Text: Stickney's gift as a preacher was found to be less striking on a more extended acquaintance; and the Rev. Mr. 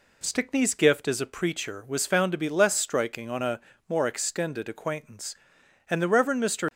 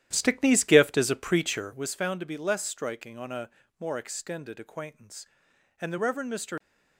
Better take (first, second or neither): first